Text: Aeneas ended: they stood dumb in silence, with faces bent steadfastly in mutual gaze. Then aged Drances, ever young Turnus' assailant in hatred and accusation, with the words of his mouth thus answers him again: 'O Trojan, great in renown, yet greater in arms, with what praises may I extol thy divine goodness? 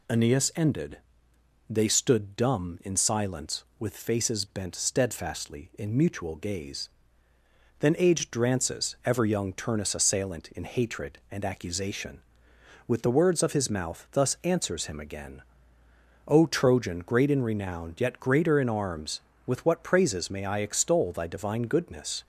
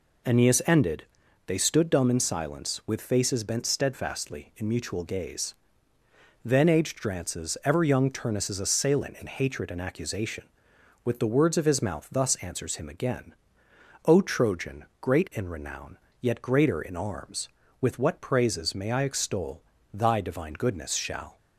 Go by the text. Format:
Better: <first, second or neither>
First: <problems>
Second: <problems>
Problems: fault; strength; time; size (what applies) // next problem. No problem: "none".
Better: first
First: none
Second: pauses between "extol" and "thy"; slight; at 19.6 s; 0.32 s long // goes on to say "Shall"; slight; from 20.9 s on; 0.44 s long